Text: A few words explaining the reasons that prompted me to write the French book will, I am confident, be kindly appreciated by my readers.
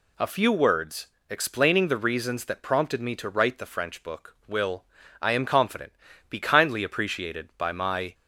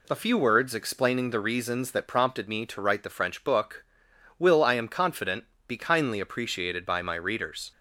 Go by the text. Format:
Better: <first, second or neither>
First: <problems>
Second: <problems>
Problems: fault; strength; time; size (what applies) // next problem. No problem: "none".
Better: second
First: pauses between "words" and "explaining"; slight; at 1.0 s; 0.20 s long // stops before "readers"; at 8.1 s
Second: none